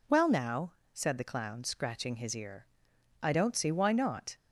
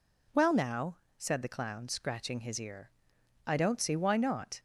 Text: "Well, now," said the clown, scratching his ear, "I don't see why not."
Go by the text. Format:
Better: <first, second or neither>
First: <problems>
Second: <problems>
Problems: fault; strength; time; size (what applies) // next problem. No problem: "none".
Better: neither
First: none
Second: none